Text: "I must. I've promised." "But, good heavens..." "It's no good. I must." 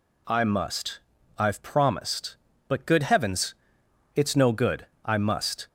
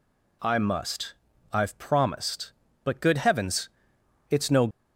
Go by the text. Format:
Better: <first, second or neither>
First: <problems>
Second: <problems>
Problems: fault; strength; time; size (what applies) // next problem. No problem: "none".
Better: first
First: none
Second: stops before "good I must"; at 4.7 s